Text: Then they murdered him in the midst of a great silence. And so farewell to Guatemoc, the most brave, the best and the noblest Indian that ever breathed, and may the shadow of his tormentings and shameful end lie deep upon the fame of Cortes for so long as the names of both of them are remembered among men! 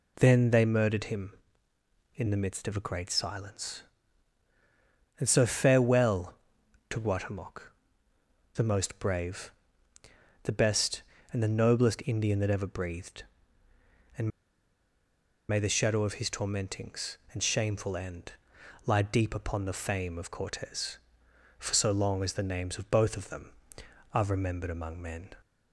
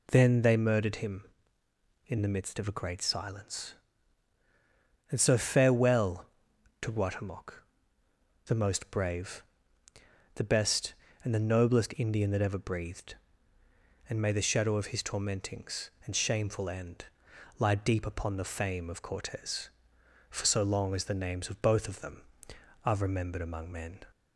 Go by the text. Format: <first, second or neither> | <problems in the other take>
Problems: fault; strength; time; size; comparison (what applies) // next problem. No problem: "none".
second | pauses between "and" and "may"; at 14.2 s; 1.2 s long // pauses between "end" and "lie"; noticeable; at 18.3 s; 0.52 s long; noticeable in the second